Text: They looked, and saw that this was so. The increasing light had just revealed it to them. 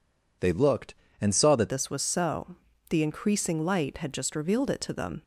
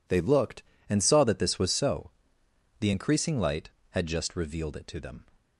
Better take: second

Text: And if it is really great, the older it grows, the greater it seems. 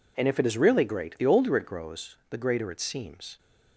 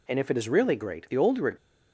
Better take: first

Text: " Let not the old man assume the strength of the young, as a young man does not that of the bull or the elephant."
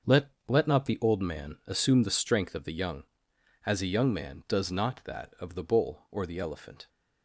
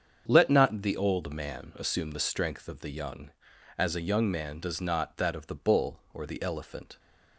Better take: second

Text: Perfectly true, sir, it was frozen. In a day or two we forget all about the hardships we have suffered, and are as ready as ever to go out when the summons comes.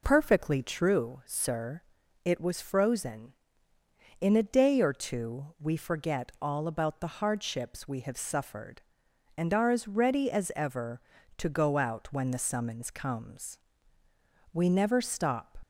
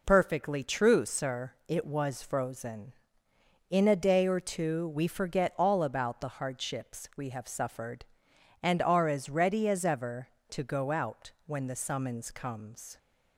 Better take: second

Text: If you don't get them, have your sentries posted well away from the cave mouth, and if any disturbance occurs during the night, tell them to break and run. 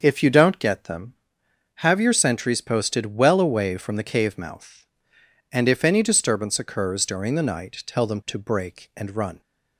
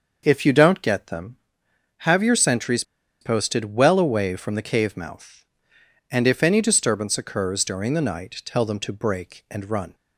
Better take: first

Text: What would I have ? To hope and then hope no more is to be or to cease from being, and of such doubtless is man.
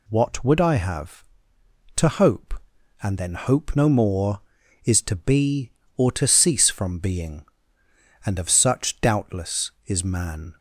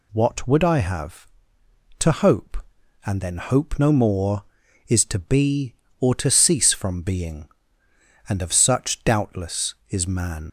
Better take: first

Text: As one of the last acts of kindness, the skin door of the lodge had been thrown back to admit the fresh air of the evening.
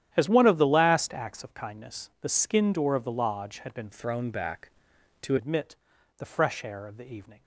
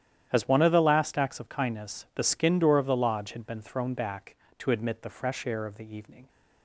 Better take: second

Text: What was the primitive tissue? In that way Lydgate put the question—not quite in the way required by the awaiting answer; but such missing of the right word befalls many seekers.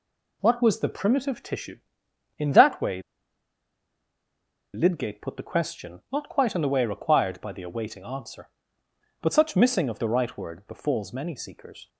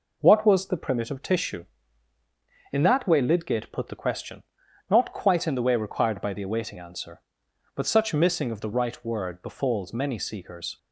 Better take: second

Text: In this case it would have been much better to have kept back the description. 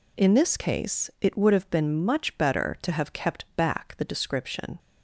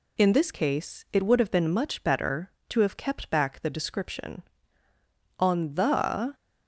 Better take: first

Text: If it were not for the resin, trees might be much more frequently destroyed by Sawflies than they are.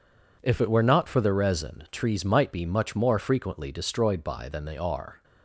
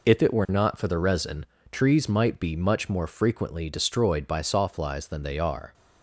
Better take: second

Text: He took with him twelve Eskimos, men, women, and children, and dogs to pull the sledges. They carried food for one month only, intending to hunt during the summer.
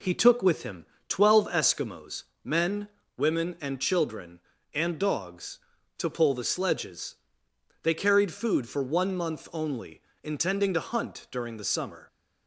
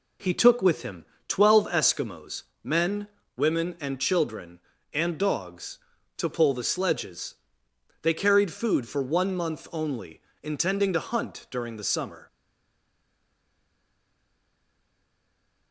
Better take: first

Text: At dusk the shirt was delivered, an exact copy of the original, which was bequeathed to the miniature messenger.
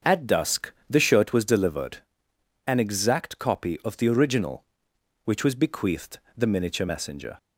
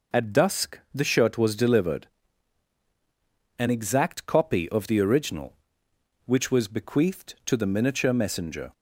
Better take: second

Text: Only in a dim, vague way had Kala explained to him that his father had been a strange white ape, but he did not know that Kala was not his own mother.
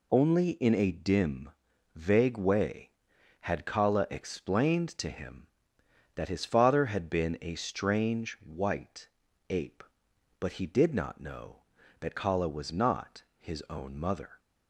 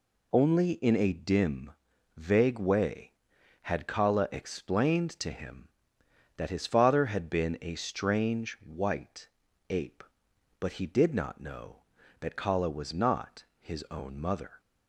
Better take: neither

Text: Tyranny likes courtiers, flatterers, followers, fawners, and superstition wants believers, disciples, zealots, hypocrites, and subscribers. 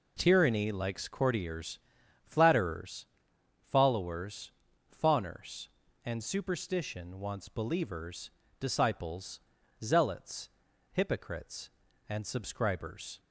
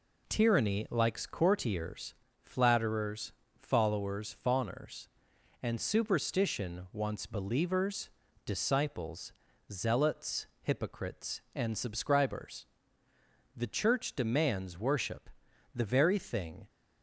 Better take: first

